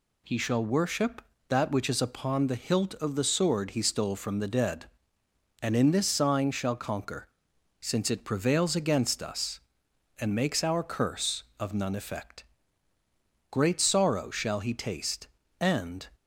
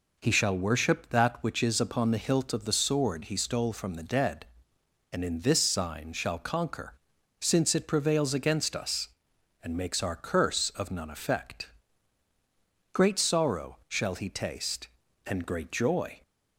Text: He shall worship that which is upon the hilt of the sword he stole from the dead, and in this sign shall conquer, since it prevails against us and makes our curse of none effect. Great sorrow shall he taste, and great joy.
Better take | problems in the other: second | stops before "great joy"; at 16.1 s

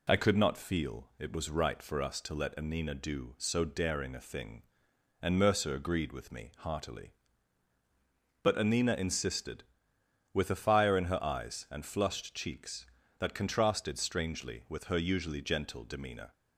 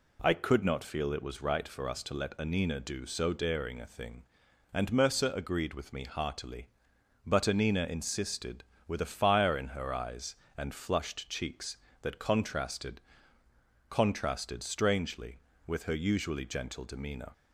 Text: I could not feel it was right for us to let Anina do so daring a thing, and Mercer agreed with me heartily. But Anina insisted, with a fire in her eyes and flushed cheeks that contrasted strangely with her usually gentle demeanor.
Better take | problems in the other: first | says "contrasted" twice; at 13.8 s

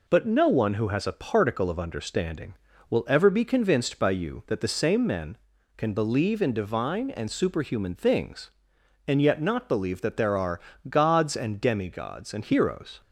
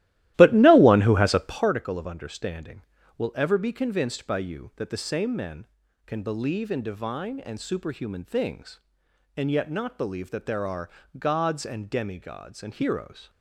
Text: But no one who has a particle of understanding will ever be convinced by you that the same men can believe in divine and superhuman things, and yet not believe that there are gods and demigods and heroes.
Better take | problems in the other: first | starts louder than the rest; strong; until 1.8 s; 15 dB // pauses between "are" and "gods"; slight; at 10.8 s; 0.28 s long; slight in the first

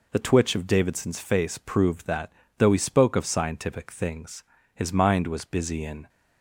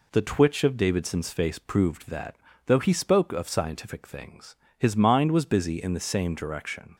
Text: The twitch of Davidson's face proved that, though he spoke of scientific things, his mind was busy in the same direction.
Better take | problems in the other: second | stops before "the same direction"; at 6.0 s

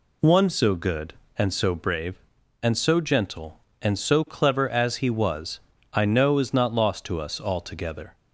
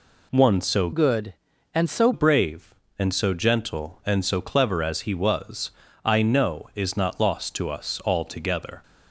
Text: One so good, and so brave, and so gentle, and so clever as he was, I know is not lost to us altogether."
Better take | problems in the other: first | changes voice from "good" to "so"; from 0.9 to 2.1 s; 1.2 s long

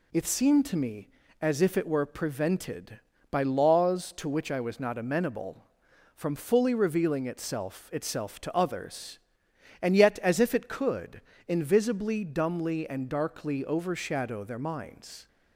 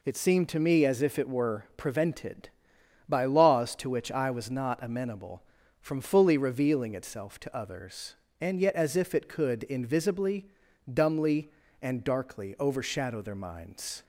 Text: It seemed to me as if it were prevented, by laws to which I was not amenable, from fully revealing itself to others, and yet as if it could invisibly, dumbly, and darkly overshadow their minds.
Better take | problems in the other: second | says "itself" twice; at 7.9 s // pauses between "could" and "invisibly"; slight; at 11.2 s; 0.26 s long

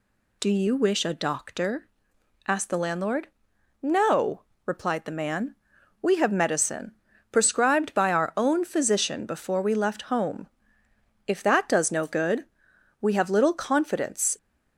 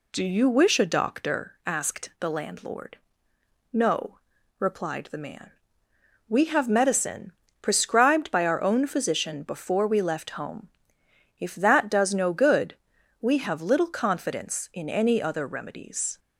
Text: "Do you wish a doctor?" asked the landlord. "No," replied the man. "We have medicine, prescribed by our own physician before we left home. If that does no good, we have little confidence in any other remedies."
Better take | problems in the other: second | stops before "in any other remedies"; at 14.3 s

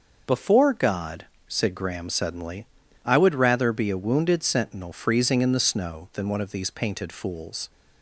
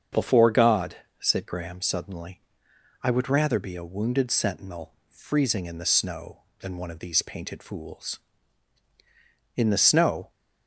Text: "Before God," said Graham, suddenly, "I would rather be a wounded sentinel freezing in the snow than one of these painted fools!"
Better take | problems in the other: first | starts louder than the rest; until 1.3 s; 7 dB // pauses between "sentinel" and "freezing"; slight; at 4.9 s; 0.16 s long // goes on to say "In the snow"; noticeable; from 9.5 s on; 0.74 s long

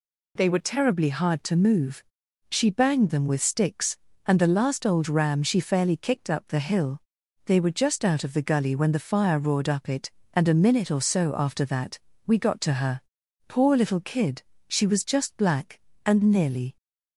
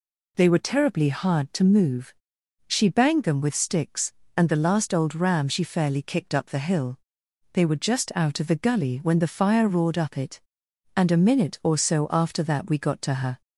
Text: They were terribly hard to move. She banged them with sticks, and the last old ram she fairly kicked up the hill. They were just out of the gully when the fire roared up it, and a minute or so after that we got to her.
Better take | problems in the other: second | pauses between "that" and "we"; slight; at 11.9 s; 0.28 s long // goes on to say "Poor little kid she was just black and nearly"; strong; from 13.4 s on; 3.2 s long

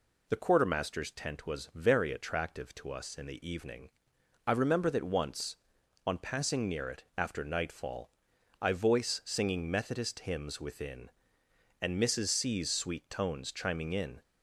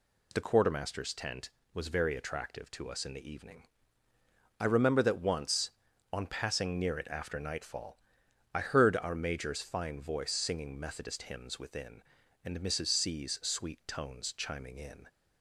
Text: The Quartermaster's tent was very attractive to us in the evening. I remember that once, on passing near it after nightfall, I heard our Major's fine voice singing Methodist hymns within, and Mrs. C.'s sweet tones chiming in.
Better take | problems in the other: second | skips "heard our Major's fine"; at 8.7 s

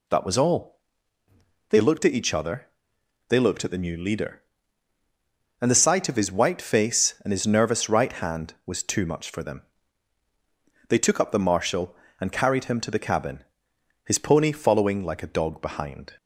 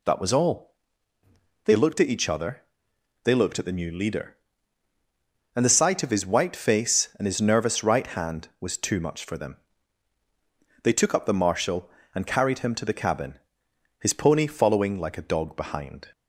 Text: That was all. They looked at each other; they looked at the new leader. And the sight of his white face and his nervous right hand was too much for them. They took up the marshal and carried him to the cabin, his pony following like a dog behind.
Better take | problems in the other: neither | none

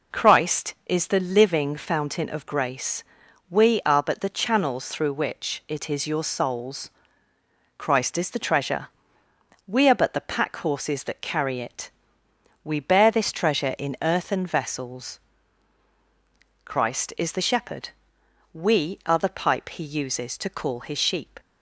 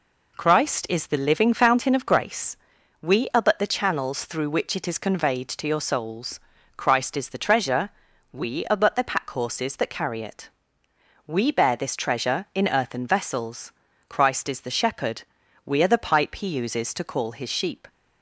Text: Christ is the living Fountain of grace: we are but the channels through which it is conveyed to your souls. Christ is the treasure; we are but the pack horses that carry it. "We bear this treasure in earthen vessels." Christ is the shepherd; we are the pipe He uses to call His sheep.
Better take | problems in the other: second | skips "conveyed to"; at 6.0 s

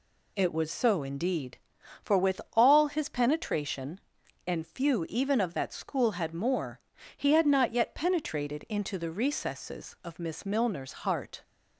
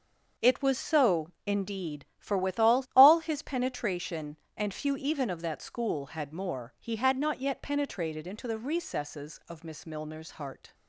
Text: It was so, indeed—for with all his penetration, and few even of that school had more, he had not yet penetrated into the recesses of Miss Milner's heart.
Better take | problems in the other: first | says "all" twice; at 2.9 s

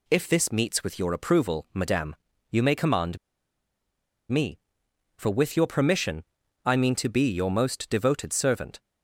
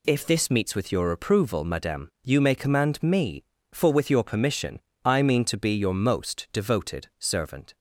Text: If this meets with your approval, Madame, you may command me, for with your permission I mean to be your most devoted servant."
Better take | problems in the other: second | pauses between "command" and "me"; at 3.1 s; 1.1 s long // pauses between "permission" and "I"; at 6.2 s; 0.42 s long; slight in the second

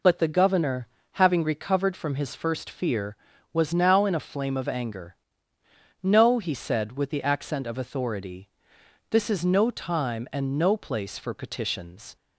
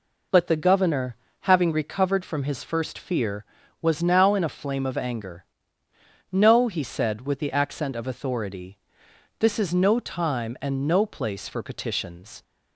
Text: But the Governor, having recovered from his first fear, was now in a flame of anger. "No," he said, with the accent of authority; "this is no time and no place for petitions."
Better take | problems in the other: neither | none

